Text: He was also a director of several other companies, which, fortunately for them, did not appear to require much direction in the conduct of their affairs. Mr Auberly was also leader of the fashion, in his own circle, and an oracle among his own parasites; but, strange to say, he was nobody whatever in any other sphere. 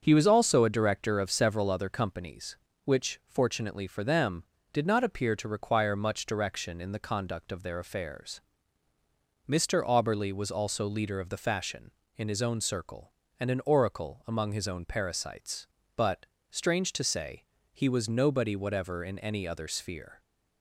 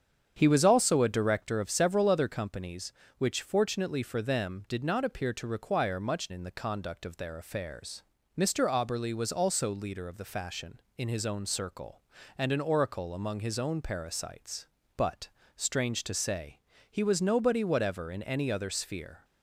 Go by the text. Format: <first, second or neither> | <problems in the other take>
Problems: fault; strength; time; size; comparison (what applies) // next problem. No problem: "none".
first | starts louder than the rest; strong; until 1.3 s; 8 dB; also in the first // skips "direction"; at 6.3 s